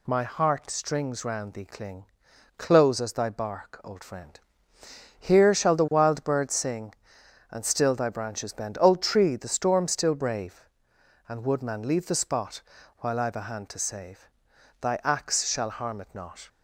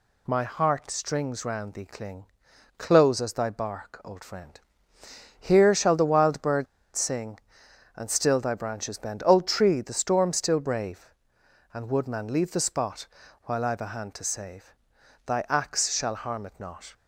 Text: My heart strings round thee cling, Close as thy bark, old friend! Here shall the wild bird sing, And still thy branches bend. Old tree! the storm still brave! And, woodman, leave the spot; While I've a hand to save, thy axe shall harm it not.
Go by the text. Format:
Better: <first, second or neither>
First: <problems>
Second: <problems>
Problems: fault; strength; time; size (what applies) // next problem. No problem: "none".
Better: first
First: none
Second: pauses between "bird" and "sing"; slight; at 6.6 s; 0.29 s long